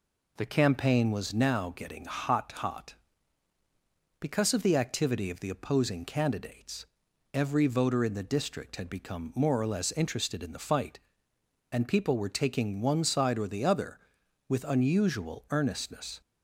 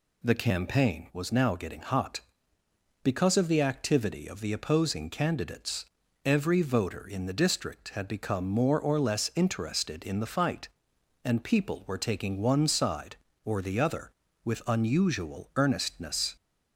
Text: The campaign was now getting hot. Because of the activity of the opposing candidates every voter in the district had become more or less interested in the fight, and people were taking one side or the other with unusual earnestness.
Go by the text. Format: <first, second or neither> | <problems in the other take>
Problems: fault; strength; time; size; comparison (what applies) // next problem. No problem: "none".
second | says "hot" twice; at 2.5 s // pauses between "candidates" and "every"; noticeable; at 6.8 s; 0.48 s long; also in the second